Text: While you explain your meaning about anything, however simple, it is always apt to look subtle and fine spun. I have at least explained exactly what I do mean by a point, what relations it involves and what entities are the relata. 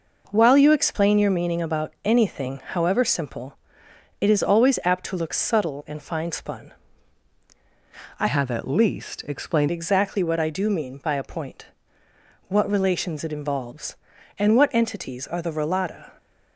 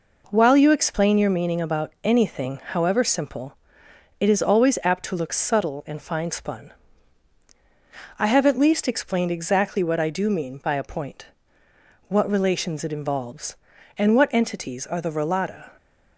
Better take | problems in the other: second | changes voice from "have" to "explained"; from 8.2 to 9.6 s; 1.4 s long

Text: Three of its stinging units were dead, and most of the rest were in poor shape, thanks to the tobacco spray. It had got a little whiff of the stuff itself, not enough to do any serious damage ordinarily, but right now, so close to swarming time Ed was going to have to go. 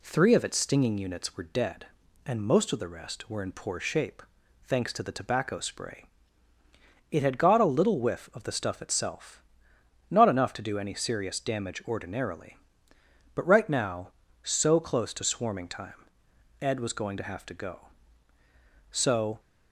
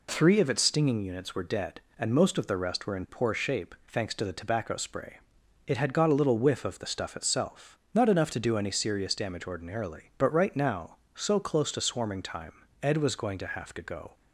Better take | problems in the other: second | pauses between "time" and "Ed"; noticeable; at 16.0 s; 0.54 s long; slight in the second // goes on to say "So"; from 18.8 s on; 0.50 s long

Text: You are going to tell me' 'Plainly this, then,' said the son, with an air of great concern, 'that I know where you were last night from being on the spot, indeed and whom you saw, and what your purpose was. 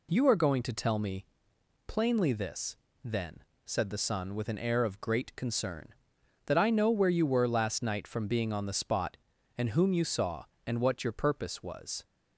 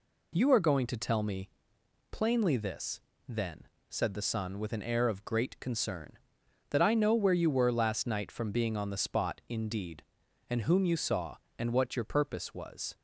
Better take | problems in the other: second | pauses between "me" and "Plainly"; noticeable; at 1.2 s; 0.62 s long; noticeable in the second // skips "indeed"; at 9.3 s

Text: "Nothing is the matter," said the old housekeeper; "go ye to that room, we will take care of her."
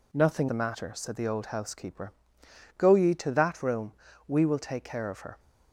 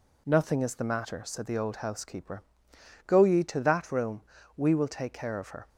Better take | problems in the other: second | skips "is"; at 0.4 s

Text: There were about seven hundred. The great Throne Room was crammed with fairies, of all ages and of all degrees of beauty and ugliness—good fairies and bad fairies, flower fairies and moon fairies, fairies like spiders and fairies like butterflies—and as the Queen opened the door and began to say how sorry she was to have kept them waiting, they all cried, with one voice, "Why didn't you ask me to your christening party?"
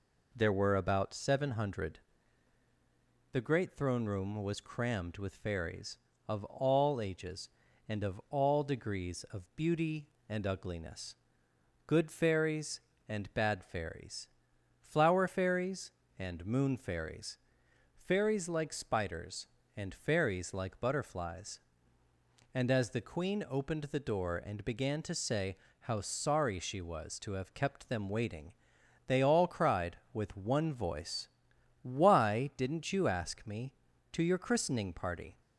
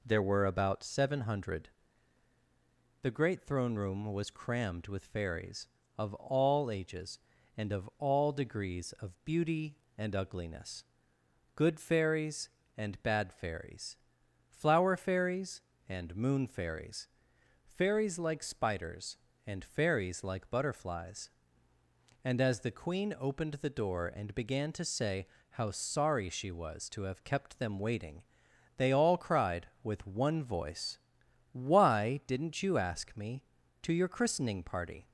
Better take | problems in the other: neither | pauses between "say" and "how"; slight; the same in both

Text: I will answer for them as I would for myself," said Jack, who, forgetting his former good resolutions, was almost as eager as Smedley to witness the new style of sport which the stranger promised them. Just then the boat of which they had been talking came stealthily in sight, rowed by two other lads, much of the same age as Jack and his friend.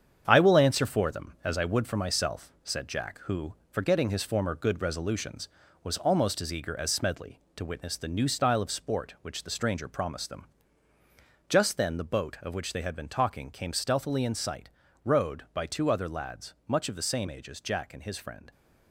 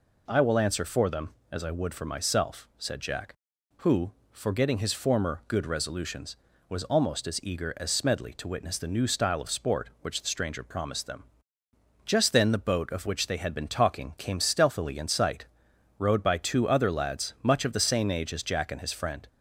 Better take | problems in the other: second | gets quieter; throughout; 6.5 dB

